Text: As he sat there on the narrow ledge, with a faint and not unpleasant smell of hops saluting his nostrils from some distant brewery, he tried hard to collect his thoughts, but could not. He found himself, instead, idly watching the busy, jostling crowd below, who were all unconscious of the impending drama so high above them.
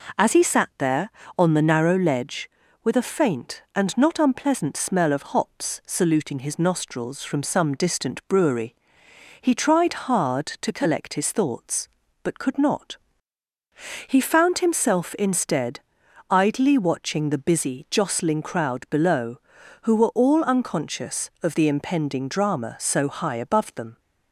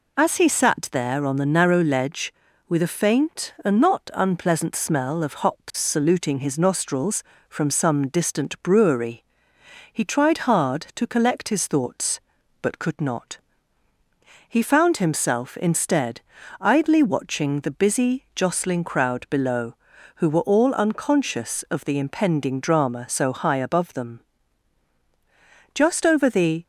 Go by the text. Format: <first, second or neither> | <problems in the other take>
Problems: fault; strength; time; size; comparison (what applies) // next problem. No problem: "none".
first | goes on to say "Just over the"; noticeable; from 25.7 s on; 0.90 s long